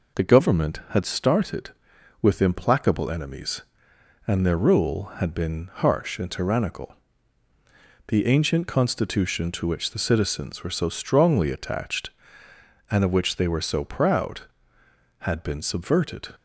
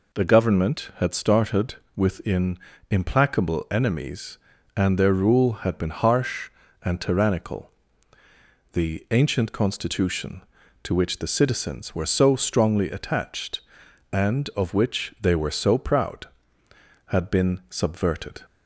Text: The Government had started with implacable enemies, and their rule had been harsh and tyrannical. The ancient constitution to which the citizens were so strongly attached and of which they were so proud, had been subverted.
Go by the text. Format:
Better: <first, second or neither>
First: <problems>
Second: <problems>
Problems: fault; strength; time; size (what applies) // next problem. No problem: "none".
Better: first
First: none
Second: says "within" for "with"; at 1.9 s